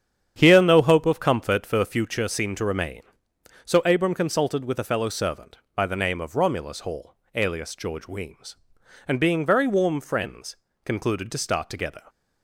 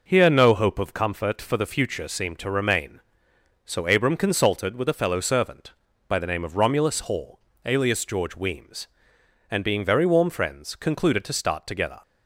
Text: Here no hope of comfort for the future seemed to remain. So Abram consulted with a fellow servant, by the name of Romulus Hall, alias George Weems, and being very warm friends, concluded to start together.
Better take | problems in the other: second | starts louder than the rest; strong; until 2.1 s; 9 dB

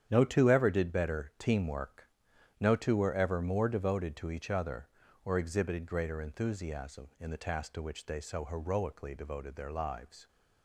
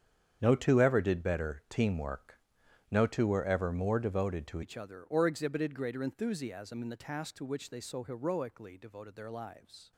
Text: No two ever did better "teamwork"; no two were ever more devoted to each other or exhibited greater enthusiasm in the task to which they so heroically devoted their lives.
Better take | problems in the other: first | starts louder than the rest; strong; until 1.4 s; 8.5 dB; strong in the first // changes voice at "each"; from 4.6 s on; 5.3 s long

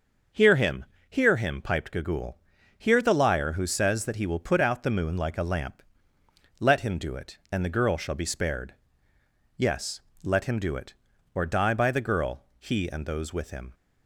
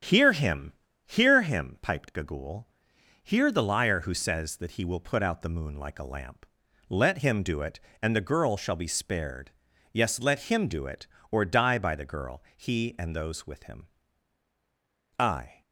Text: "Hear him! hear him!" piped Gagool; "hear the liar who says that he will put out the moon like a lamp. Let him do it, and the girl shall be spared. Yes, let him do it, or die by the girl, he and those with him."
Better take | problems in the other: first | starts louder than the rest; strong; until 1.3 s; 9 dB; also in the first // goes on to say "I"; slight; from 15.1 s on; 0.44 s long

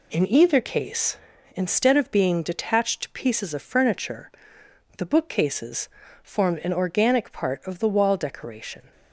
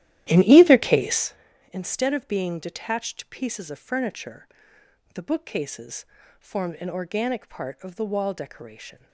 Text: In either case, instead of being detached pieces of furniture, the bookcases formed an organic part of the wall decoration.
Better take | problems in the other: first | starts louder than the rest; strong; until 1.3 s; 13 dB // pauses between "bookcases" and "formed"; slight; at 6.0 s; 0.34 s long; slight in the first

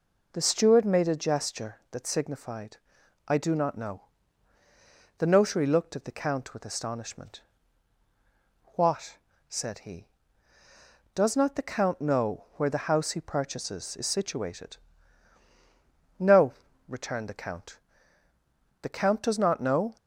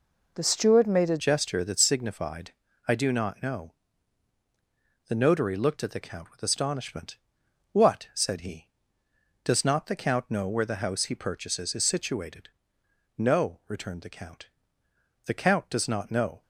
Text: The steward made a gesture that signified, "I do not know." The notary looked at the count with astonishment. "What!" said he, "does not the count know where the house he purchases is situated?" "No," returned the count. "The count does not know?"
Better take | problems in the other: first | changes voice at "gesture"; from 1.1 s on; 15.3 s long

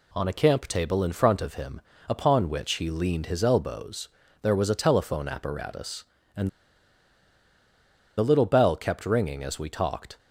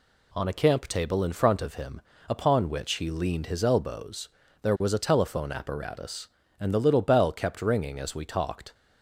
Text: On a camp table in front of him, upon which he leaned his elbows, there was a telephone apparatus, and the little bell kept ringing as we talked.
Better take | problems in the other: second | pauses between "and" and "the"; strong; at 6.4 s; 1.6 s long

